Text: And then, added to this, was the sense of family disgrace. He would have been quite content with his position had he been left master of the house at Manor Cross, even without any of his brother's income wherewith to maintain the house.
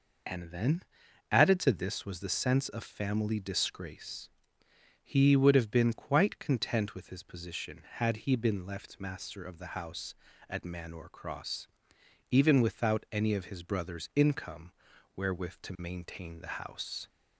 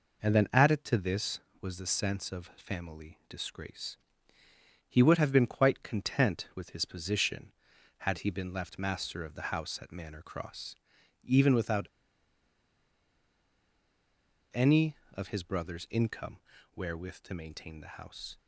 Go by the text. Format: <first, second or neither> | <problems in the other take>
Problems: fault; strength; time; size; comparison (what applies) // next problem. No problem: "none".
first | pauses between "without" and "any"; strong; at 11.8 s; 2.6 s long // pauses between "income" and "wherewith"; at 16.3 s; 0.38 s long; also in the first